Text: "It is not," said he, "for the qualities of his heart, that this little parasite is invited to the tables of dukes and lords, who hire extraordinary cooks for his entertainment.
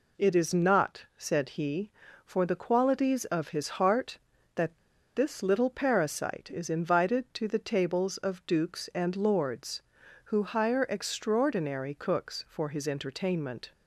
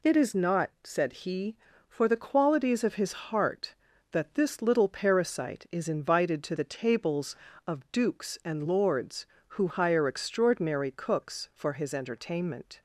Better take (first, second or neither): second